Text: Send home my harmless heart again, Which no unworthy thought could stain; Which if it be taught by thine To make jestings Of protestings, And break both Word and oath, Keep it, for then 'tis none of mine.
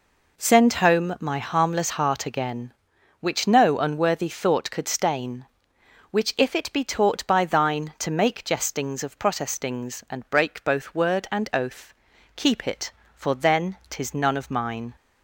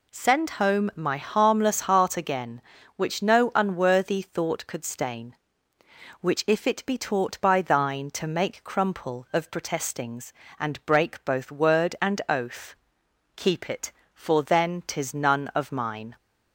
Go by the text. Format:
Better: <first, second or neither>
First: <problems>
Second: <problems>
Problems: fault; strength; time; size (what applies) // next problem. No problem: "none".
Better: first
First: none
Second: says "crumple" for "jestings"; at 8.6 s